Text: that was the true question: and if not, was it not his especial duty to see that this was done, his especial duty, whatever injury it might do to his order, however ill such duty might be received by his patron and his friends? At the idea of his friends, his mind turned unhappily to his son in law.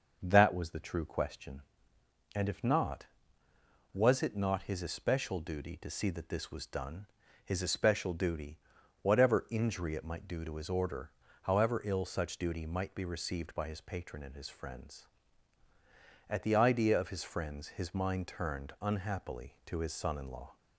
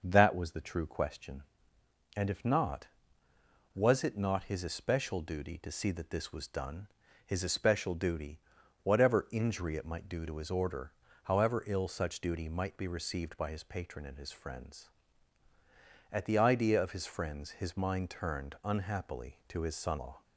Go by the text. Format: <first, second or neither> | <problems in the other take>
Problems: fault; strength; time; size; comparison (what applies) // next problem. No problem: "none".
first | starts louder than the rest; until 1.0 s; 6.5 dB; also in the first // skips "in"; at 19.9 s